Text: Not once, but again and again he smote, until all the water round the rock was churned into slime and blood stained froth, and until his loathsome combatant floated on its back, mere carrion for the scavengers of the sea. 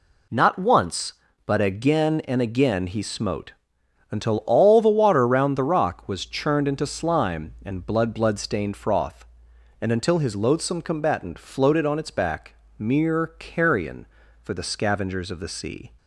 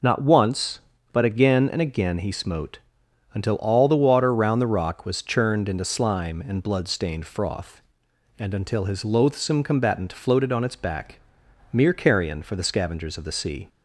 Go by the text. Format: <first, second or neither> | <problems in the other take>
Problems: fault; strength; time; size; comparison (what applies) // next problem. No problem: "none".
second | says "blood" twice; at 8.1 s